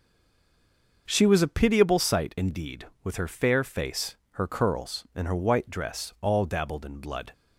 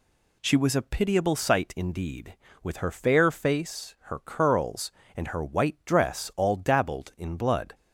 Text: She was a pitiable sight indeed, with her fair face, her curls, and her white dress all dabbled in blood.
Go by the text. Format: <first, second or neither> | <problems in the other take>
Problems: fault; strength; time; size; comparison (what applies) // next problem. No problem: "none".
second | stays silent before the first word; until 1.0 s; 1.0 s long // starts louder than the rest; noticeable; until 2.0 s; 6 dB